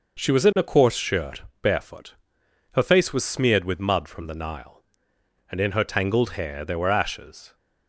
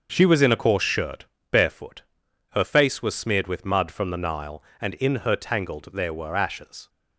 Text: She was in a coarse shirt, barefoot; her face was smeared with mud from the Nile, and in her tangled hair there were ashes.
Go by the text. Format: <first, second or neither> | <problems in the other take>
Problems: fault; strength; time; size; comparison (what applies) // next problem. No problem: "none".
first | starts louder than the rest; until 1.1 s; 6.5 dB // skips "hair"; at 5.9 s